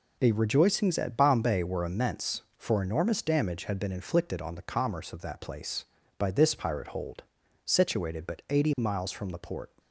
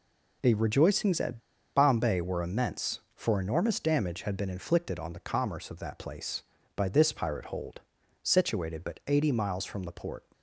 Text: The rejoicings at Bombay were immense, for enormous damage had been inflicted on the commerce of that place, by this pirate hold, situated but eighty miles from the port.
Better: first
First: none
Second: pauses between "at" and "Bombay"; slight; at 1.3 s; 0.36 s long

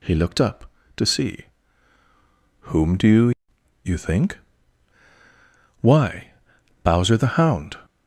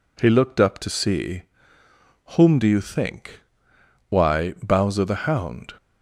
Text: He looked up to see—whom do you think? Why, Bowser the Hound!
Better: second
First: says "you" twice; at 3.8 s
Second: none

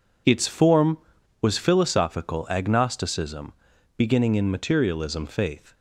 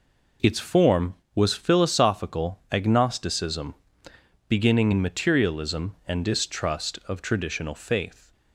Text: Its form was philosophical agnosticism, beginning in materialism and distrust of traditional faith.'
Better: second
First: skips "and distrust of traditional"; at 5.2 s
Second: none

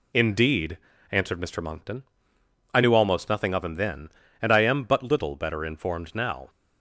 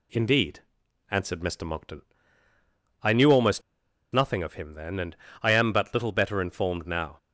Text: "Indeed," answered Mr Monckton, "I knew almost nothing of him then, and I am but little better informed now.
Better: first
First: none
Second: pauses between "almost" and "nothing"; noticeable; at 3.6 s; 0.51 s long // pauses between "and" and "I"; slight; at 5.1 s; 0.26 s long

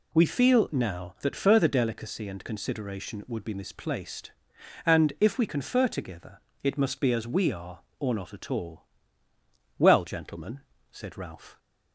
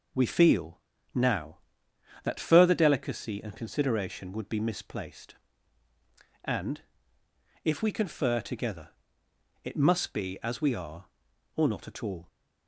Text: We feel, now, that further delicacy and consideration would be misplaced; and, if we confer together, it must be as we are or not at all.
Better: second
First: goes on to say "Well gentlemen said Ralph"; strong; from 9.7 s on; 1.8 s long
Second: none

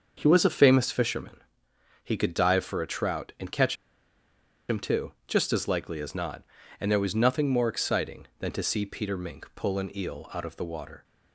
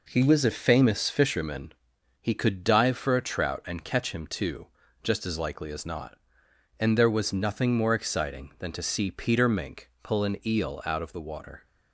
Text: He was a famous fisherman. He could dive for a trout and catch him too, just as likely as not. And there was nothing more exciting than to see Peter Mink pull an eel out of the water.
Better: second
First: starts louder than the rest; until 1.1 s; 6.5 dB // pauses between "catch" and "him"; noticeable; at 3.7 s; 0.93 s long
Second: none

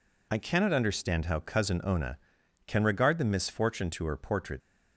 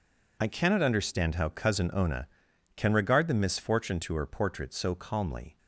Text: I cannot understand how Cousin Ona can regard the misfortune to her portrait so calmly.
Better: second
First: stops before "so calmly"; at 4.6 s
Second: none

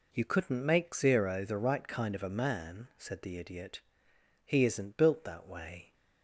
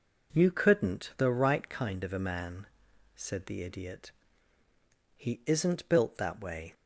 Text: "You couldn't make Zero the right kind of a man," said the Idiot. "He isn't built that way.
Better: first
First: none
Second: skips "make Zero"; at 1.1 s

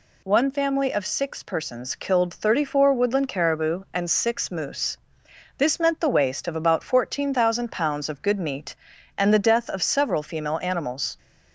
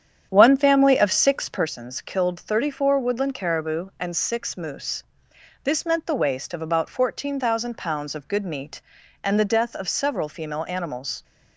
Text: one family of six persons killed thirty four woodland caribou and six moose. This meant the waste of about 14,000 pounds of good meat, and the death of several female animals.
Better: first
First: none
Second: starts louder than the rest; strong; until 1.8 s; 9 dB

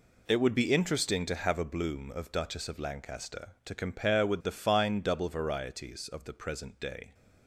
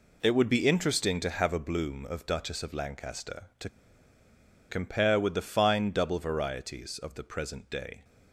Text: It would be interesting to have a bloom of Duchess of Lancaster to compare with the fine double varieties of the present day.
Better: first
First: none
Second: pauses between "to" and "compare"; at 3.6 s; 0.99 s long

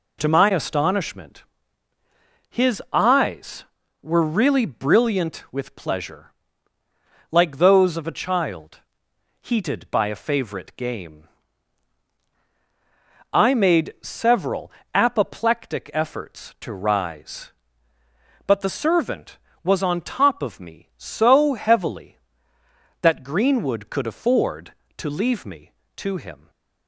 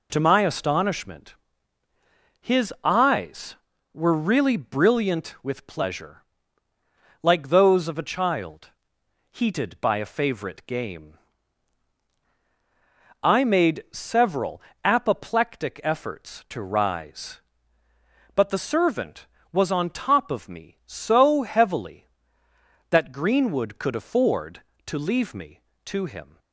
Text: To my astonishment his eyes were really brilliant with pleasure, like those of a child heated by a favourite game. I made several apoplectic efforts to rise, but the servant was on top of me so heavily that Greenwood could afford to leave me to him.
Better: neither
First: pauses between "astonishment" and "his"; at 1.4 s; 1.0 s long // pauses between "child" and "heated"; noticeable; at 8.7 s; 0.60 s long // pauses between "several" and "apoplectic"; slight; at 14.6 s; 0.24 s long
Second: pauses between "astonishment" and "his"; at 1.3 s; 1.0 s long // pauses between "child" and "heated"; noticeable; at 8.6 s; 0.60 s long // pauses between "several" and "apoplectic"; slight; at 14.5 s; 0.24 s long

